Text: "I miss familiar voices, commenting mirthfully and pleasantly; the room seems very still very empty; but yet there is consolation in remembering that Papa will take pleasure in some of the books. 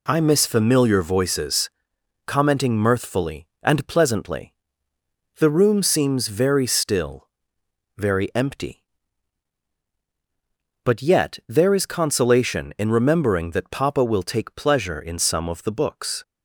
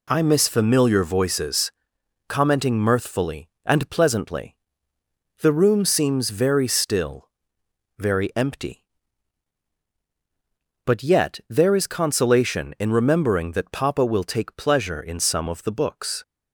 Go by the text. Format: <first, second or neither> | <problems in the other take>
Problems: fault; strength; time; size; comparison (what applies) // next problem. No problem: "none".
neither | pauses between "still" and "very"; noticeable; the same in both